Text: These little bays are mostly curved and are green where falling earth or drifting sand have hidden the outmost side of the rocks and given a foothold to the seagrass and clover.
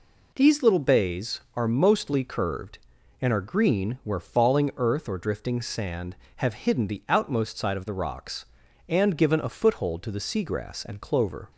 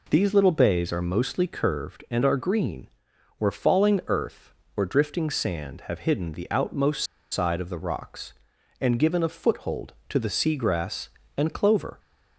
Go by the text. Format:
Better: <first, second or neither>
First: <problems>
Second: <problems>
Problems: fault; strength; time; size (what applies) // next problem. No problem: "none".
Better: first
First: none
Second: pauses between "green" and "where"; noticeable; at 2.8 s; 0.52 s long // pauses between "outmost" and "side"; slight; at 7.0 s; 0.26 s long